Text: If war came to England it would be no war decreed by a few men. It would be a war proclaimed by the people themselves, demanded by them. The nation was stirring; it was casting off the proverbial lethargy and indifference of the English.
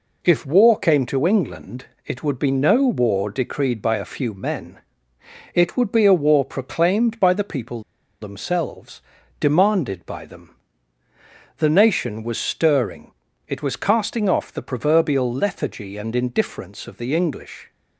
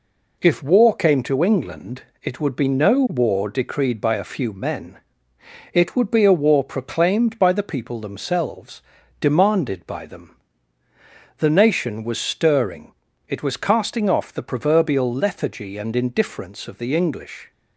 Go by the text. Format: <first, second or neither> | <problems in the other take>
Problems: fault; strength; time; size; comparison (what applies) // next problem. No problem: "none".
second | pauses between "England" and "it"; slight; at 1.8 s; 0.20 s long; slight in the second // pauses between "people" and "themselves"; at 7.8 s; 0.40 s long